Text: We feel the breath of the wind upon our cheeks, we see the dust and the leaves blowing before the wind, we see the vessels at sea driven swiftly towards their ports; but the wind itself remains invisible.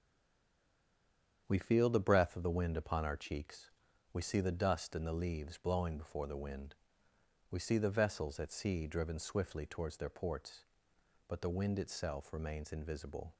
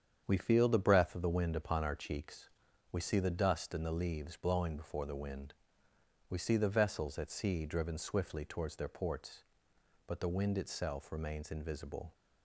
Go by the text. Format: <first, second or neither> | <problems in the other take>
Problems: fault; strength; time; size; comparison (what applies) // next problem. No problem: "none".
second | stays silent before the first word; noticeable; until 1.4 s; 1.4 s long // starts louder than the rest; strong; until 2.4 s; 8 dB; strong in the second